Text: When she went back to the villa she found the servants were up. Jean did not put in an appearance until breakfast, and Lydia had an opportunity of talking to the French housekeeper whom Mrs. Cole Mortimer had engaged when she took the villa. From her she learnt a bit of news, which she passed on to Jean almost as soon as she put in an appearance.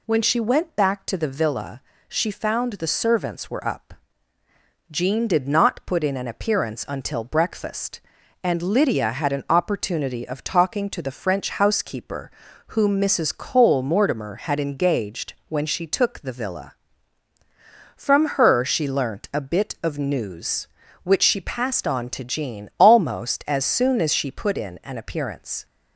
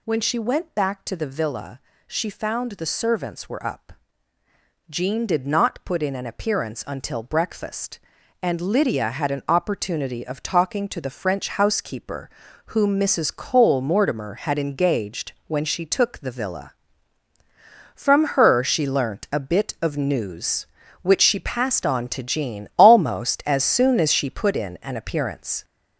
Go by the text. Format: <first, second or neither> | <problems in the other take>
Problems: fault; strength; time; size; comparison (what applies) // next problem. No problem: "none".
first | gets louder; noticeable; throughout; 6 dB // pauses between "villa" and "she"; slight; at 1.7 s; 0.26 s long; slight in the first // pauses between "housekeeper" and "whom"; at 12.2 s; 0.38 s long; also in the first // pauses between "engaged" and "when"; slight; at 15.3 s; 0.16 s long; slight in the first